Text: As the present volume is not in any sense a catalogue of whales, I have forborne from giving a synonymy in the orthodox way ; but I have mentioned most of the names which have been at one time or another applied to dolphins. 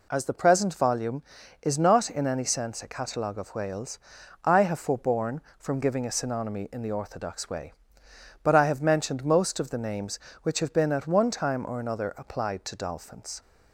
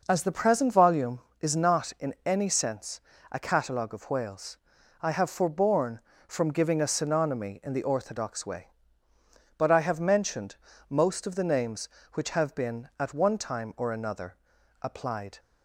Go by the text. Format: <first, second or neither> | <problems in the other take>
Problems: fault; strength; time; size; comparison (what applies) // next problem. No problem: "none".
first | pauses between "sense" and "a"; slight; at 3.0 s; 0.30 s long // pauses between "mentioned" and "most"; slight; at 10.5 s; 0.34 s long // pauses between "another" and "applied"; at 14.3 s; 0.44 s long // stops before "to dolphins"; at 15.3 s